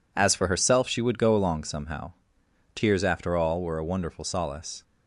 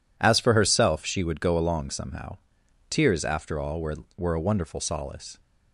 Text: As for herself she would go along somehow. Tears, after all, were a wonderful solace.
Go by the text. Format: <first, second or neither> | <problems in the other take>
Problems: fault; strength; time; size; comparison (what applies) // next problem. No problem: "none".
first | says "were" twice; at 4.1 s